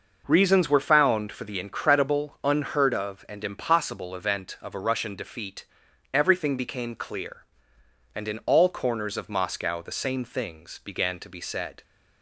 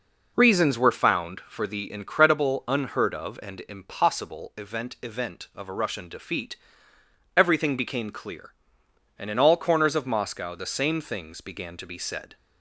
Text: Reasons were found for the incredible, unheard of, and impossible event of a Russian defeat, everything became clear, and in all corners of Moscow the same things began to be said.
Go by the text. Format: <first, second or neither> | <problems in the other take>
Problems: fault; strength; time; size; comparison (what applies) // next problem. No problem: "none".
first | says "event" twice; at 5.0 s